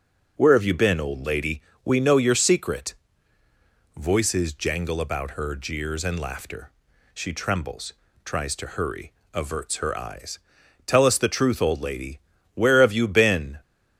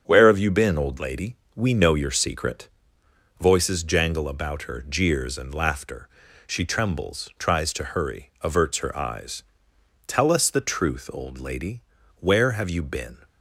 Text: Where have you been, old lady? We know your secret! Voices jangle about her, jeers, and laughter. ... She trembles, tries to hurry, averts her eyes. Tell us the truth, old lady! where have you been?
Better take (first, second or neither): neither